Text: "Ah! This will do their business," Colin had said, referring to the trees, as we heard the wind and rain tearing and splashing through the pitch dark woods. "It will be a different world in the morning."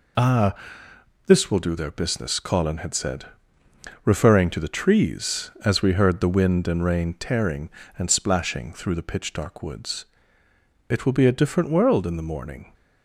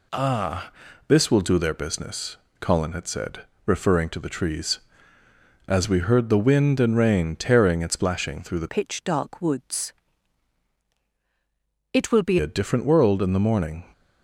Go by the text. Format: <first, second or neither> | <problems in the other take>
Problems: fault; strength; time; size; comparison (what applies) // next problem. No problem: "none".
first | changes voice from "pitch" to "be"; from 8.6 to 12.3 s; 3.7 s long